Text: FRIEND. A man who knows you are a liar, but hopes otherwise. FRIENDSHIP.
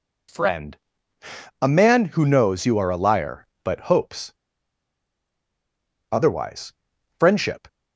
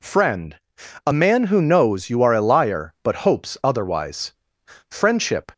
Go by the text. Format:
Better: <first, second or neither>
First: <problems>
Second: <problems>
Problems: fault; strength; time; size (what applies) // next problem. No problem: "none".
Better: second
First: pauses between "hopes" and "otherwise"; strong; at 4.3 s; 1.8 s long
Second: none